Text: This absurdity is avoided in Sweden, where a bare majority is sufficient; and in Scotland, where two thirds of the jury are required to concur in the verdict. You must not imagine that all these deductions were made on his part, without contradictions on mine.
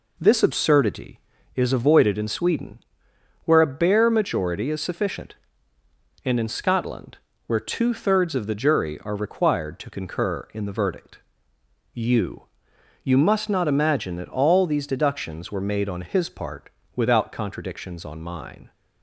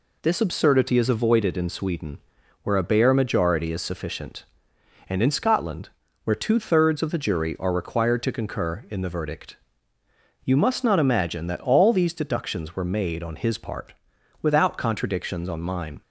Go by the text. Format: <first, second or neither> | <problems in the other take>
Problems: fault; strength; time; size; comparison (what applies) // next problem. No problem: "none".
second | says "You" twice; at 13.0 s